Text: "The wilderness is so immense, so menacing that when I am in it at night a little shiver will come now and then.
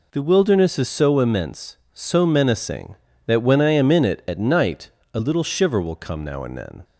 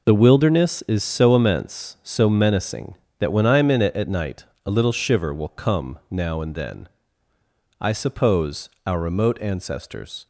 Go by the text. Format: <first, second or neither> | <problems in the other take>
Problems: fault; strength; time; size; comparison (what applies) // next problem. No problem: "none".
first | pauses between "night" and "a"; slight; at 4.4 s; 0.18 s long; slight in the first // goes on to say "I suppose our remote ancestors"; strong; from 7.8 s on; 2.4 s long